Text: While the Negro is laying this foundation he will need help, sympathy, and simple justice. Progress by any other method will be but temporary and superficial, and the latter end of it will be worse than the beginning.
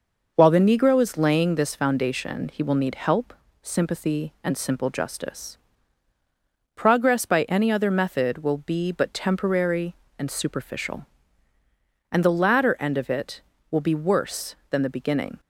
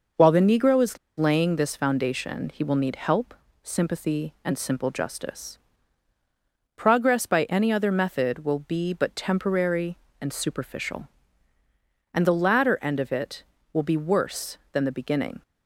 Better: first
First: none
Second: pauses between "is" and "laying"; slight; at 0.9 s; 0.20 s long

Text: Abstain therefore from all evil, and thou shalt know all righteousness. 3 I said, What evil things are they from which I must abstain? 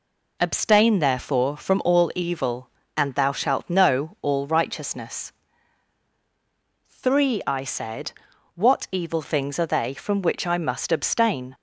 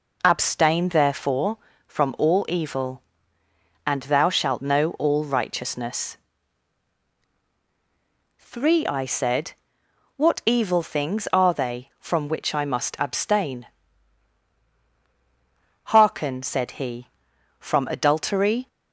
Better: first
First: none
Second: goes on to say "Hearken said he from adultery"; strong; from 15.8 s on; 2.8 s long

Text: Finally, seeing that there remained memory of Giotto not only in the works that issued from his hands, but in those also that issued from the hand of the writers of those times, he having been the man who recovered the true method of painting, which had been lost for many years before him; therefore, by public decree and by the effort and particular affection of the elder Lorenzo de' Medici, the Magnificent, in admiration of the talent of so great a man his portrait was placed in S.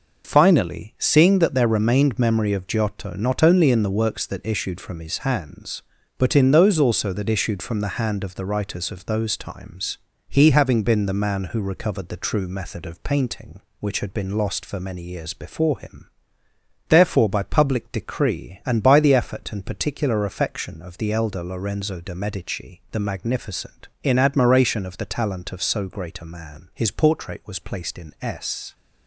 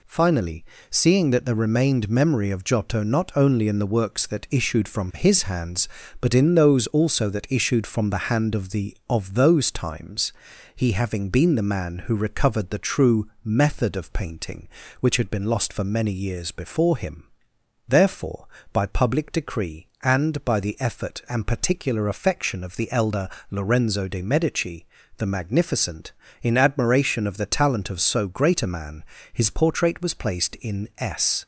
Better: first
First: none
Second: skips "writers"; at 9.0 s // pauses between "elder" and "Lorenzo"; slight; at 23.2 s; 0.22 s long // pauses between "man" and "his"; slight; at 29.0 s; 0.30 s long

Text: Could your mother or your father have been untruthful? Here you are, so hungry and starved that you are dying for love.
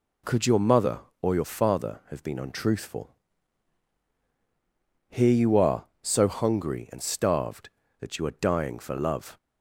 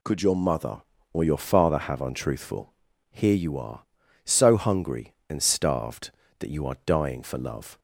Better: first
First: none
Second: skips "been"; at 2.0 s

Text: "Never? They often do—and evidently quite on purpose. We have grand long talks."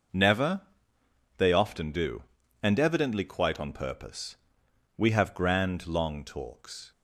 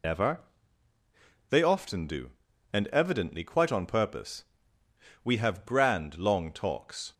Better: first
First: none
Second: loses the start of "Never"; at 0.0 s; 120 ms

